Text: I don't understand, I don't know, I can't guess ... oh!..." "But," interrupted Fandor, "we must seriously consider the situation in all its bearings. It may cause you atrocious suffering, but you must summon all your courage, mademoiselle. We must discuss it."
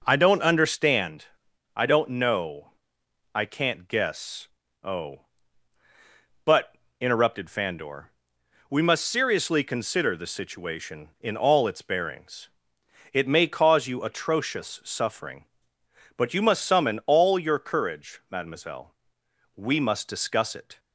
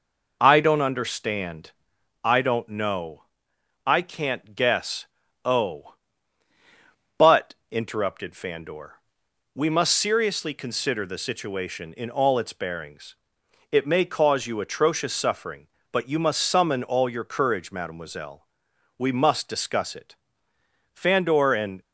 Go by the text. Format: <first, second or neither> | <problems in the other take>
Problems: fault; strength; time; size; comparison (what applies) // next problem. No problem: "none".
first | goes on to say "Fandor and"; noticeable; from 20.9 s on; 0.88 s long